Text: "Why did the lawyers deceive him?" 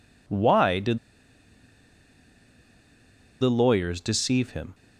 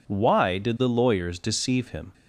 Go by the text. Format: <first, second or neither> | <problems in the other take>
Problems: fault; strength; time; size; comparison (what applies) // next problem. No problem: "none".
second | pauses between "did" and "the"; strong; at 0.9 s; 2.4 s long